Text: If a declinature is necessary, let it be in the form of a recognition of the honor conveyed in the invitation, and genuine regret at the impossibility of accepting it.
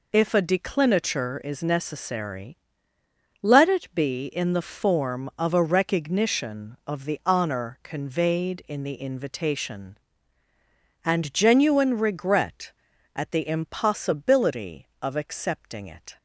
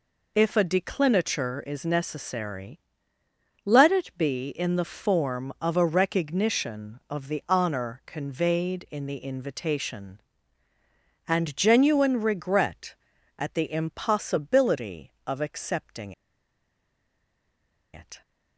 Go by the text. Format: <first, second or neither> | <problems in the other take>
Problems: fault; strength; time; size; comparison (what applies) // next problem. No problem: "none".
first | pauses between "accepting" and "it"; strong; at 16.1 s; 1.8 s long